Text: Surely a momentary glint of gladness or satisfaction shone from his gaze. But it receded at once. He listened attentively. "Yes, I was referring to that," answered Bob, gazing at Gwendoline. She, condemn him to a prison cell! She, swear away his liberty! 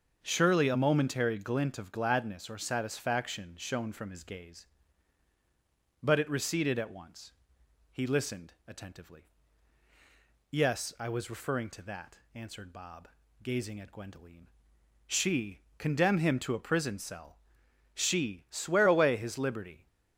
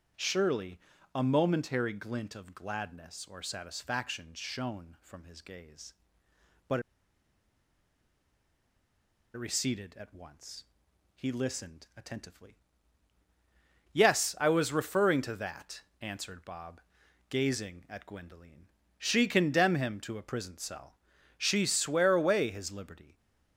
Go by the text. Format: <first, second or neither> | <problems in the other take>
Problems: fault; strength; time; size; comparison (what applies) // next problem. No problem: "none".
first | starts louder than the rest; strong; until 1.4 s; 8 dB; also in the first // pauses between "Surely" and "a"; slight; at 0.7 s; 0.34 s long // pauses between "But" and "it"; strong; at 6.7 s; 2.5 s long